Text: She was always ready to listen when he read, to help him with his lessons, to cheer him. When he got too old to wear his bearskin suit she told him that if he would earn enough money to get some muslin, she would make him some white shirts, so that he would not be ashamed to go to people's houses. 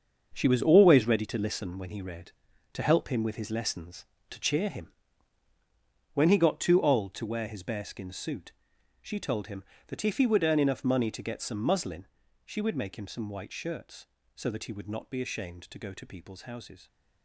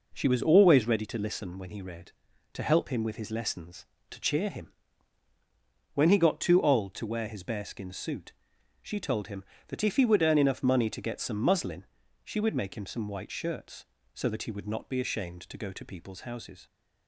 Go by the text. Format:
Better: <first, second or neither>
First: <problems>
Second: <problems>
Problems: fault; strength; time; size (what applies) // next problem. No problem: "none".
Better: second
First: gets quieter; strong; throughout; 10 dB // pauses between "suit" and "she"; noticeable; at 8.5 s; 0.52 s long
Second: pauses between "suit" and "she"; noticeable; at 8.3 s; 0.52 s long